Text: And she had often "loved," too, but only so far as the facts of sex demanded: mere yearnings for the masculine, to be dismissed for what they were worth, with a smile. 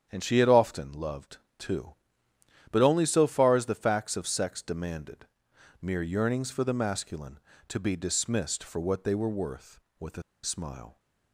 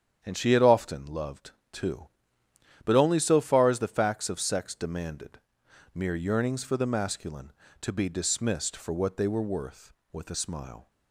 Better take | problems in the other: second | starts louder than the rest; strong; until 1.1 s; 8.5 dB; strong in the second // pauses between "a" and "smile"; slight; at 10.2 s; 0.21 s long

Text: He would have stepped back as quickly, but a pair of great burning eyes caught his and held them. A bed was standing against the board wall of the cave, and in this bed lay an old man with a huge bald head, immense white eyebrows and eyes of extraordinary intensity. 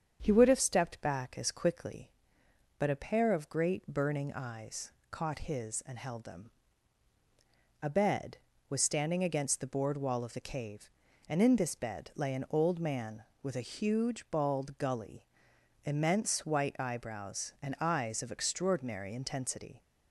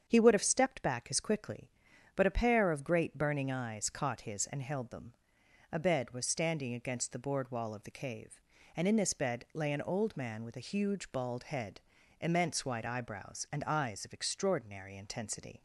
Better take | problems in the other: second | starts louder than the rest; strong; until 1.2 s; 7.5 dB; strong in the second // pauses between "eyes" and "caught"; slight; at 4.9 s; 0.18 s long // says "gully" for "head"; at 14.7 s

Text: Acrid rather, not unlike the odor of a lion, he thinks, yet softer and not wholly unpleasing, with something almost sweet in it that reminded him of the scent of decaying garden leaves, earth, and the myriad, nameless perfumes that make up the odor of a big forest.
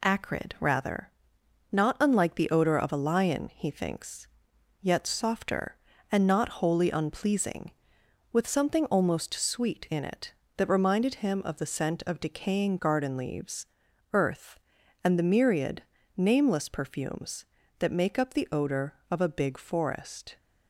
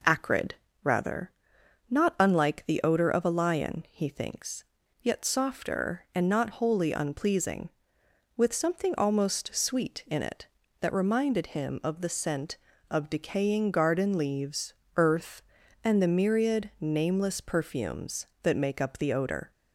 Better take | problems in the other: first | pauses between "Acrid" and "rather"; slight; at 0.5 s; 0.26 s long // stops before "of a big forest"; at 19.5 s

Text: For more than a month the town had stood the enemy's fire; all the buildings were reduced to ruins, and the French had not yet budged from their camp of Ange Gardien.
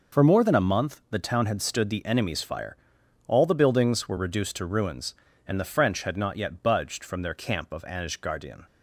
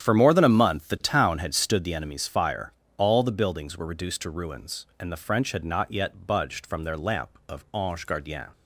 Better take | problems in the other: first | starts louder than the rest; strong; until 1.0 s; 9.5 dB // says "lamp" for "camp"; at 6.9 s

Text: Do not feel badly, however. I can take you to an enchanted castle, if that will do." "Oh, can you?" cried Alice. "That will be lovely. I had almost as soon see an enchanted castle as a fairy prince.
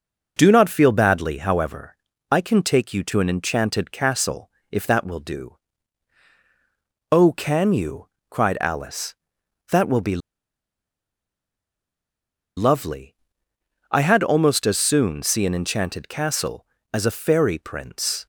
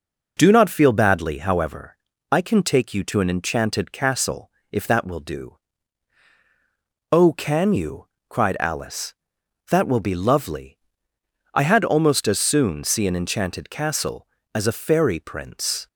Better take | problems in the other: second | pauses between "be" and "lovely"; strong; at 10.2 s; 2.3 s long

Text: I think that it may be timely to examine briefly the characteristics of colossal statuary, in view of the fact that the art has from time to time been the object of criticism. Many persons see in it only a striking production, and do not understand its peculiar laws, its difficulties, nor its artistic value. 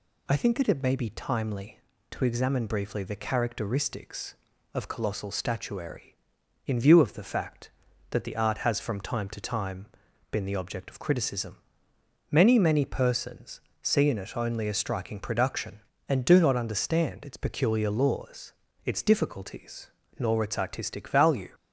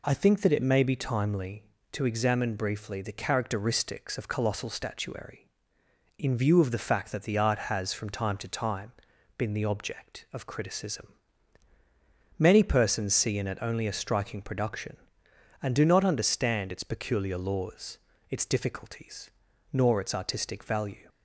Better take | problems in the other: second | pauses between "time" and "been"; at 9.8 s; 0.44 s long; noticeable in the second // says "Many" twice; at 12.5 s // pauses between "persons" and "see"; slight; at 13.6 s; 0.22 s long

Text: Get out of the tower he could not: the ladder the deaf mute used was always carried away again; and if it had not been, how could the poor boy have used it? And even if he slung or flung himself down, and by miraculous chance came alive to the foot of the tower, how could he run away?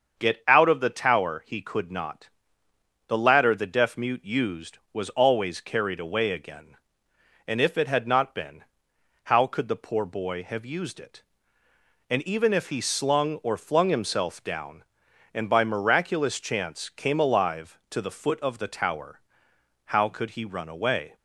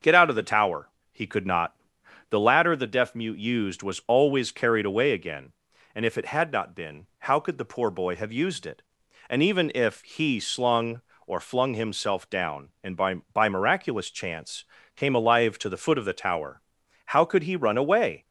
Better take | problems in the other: first | starts louder than the rest; until 1.2 s; 6.5 dB; also in the first // pauses between "tower" and "he"; slight; at 0.8 s; 0.24 s long // says "by" twice; at 13.3 s // pauses between "chance" and "came"; slight; at 14.6 s; 0.32 s long

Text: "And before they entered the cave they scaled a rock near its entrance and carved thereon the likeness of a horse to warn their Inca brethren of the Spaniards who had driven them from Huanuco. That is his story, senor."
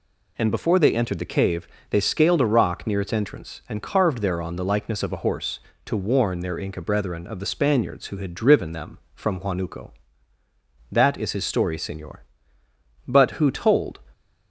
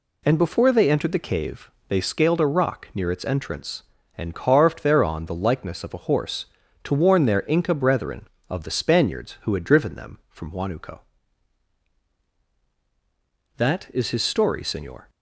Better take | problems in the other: second | pauses between "cave" and "they"; slight; at 1.6 s; 0.24 s long; slight in the second // goes on to say "But who told"; noticeable; from 13.0 s on; 0.92 s long

